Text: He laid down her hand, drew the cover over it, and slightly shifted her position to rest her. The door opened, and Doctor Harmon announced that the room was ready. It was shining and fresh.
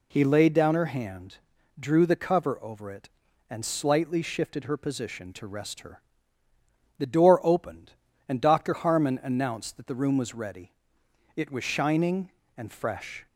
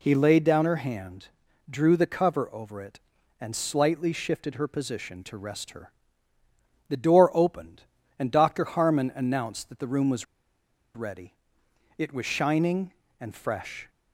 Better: first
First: none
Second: pauses between "was" and "ready"; noticeable; at 10.2 s; 0.70 s long

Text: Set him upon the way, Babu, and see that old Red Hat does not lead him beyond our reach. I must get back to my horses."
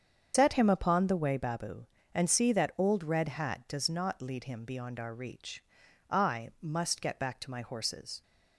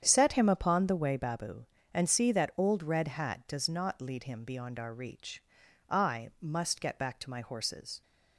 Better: second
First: loses the start of "Set"; at 0.3 s; 115 ms // starts louder than the rest; strong; until 1.3 s; 7.5 dB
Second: starts louder than the rest; strong; until 1.0 s; 8.5 dB

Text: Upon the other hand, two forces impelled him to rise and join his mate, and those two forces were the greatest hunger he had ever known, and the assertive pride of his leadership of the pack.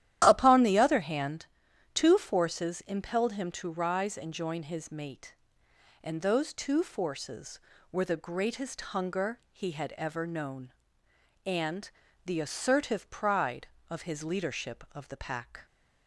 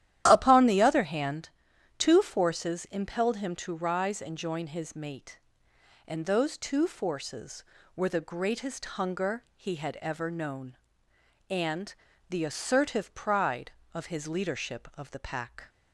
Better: neither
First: starts louder than the rest; strong; until 1.2 s; 12 dB // pauses between "and" and "the"; slight; at 11.9 s; 0.34 s long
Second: starts louder than the rest; strong; until 1.2 s; 12 dB // pauses between "and" and "the"; slight; at 11.9 s; 0.34 s long

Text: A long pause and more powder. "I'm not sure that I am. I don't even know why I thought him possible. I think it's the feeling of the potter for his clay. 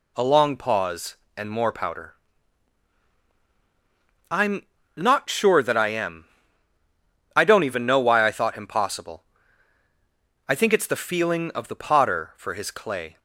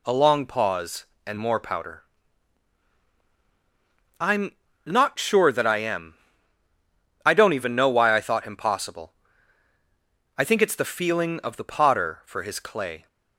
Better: neither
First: pauses between "I'm" and "not"; slight; at 4.6 s; 0.30 s long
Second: pauses between "I'm" and "not"; slight; at 4.5 s; 0.30 s long

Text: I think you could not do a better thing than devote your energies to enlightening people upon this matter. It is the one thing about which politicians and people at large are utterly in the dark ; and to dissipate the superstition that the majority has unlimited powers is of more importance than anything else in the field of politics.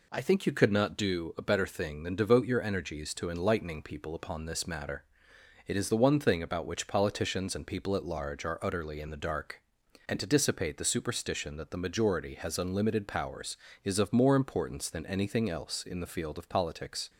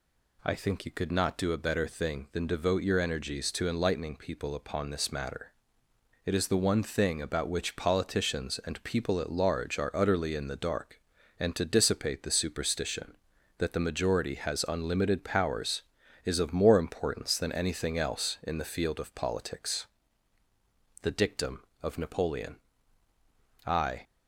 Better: first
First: none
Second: goes on to say "The dictum of Napoleon I"; strong; from 21.0 s on; 3.0 s long

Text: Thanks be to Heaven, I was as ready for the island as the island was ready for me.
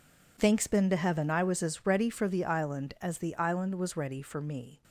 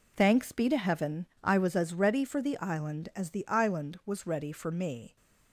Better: second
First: says "been" for "be"; at 0.6 s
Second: none

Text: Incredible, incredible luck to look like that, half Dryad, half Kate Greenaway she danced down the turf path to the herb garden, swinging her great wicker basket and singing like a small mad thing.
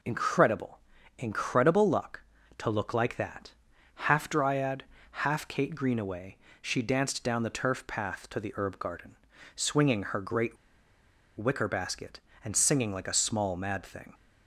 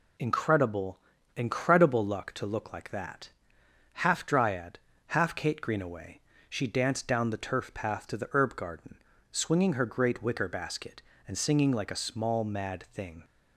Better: second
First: pauses between "Greenaway" and "she"; slight; at 6.3 s; 0.26 s long // pauses between "great" and "wicker"; noticeable; at 10.5 s; 0.81 s long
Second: pauses between "Greenaway" and "she"; slight; at 6.2 s; 0.28 s long

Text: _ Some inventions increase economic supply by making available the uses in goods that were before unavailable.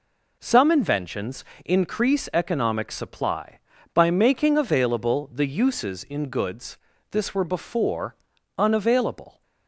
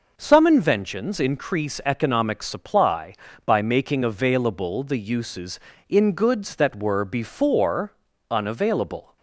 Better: second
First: pauses between "inventions" and "increase"; slight; at 1.4 s; 0.20 s long // says "this" for "that"; at 7.1 s // pauses between "before" and "unavailable"; at 8.1 s; 0.42 s long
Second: pauses between "before" and "unavailable"; at 7.9 s; 0.38 s long

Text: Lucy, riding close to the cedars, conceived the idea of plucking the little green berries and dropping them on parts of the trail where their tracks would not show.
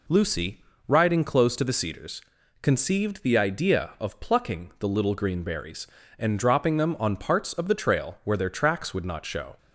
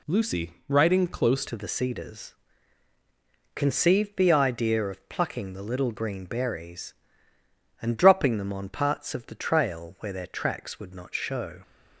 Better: first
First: none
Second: changes voice at "to"; from 1.4 s on; 10.2 s long

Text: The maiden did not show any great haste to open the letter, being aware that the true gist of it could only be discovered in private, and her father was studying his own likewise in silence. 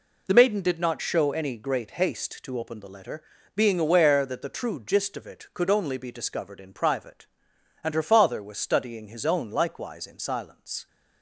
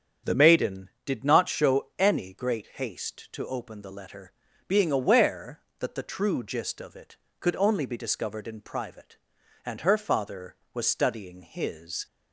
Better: first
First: none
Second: starts louder than the rest; strong; until 1.4 s; 8 dB // stops before "own likewise in silence"; at 12.0 s

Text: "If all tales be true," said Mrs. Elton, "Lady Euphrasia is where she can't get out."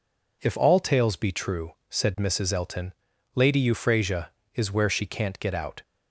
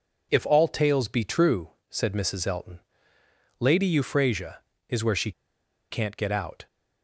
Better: first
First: none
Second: pauses between "she" and "can't"; noticeable; at 5.3 s; 0.59 s long

